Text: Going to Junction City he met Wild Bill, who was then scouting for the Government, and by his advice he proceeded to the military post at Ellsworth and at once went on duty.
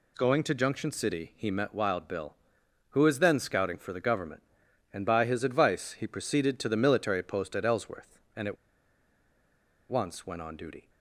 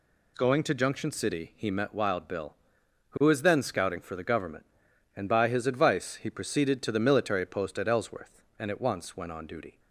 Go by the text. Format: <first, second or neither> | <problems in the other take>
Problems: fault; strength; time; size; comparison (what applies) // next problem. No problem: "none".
second | pauses between "at" and "once"; strong; at 8.5 s; 1.3 s long